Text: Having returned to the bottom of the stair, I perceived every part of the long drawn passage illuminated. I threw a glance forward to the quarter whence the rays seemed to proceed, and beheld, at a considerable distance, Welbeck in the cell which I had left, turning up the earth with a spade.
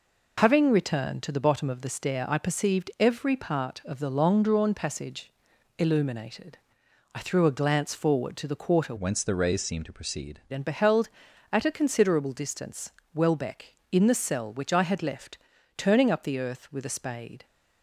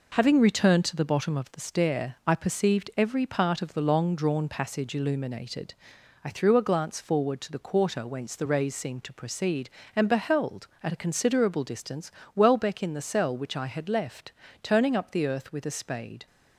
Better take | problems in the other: second | pauses between "passage" and "illuminated"; noticeable; at 5.3 s; 0.46 s long // changes voice from "whence" to "proceed"; from 8.9 to 10.3 s; 1.4 s long

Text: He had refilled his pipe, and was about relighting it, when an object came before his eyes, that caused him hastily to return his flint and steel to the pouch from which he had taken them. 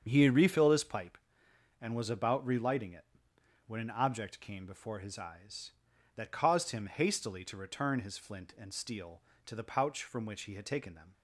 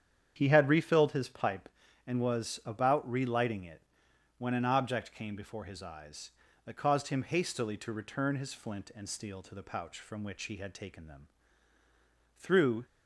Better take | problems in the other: first | starts louder than the rest; strong; until 1.3 s; 8.5 dB; strong in the first // goes on to say "Through"; slight; from 12.3 s on; 0.48 s long

